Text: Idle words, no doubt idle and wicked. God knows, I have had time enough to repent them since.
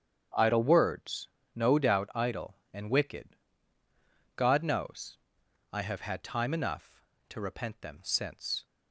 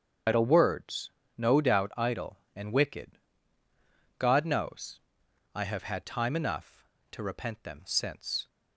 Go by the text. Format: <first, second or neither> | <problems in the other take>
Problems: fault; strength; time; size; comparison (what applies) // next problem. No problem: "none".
first | loses the start of "Idle"; at 0.2 s; 130 ms // starts louder than the rest; strong; until 1.5 s; 8 dB; strong in the first